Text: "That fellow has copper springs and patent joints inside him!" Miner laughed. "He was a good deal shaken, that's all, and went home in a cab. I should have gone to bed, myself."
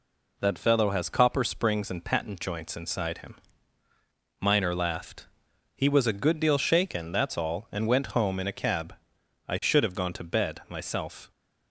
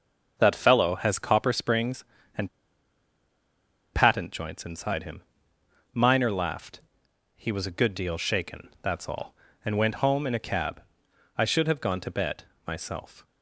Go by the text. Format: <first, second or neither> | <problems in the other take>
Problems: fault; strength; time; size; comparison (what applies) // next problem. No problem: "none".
first | starts louder than the rest; until 1.3 s; 6 dB // pauses between "and" and "patent"; strong; at 2.4 s; 1.4 s long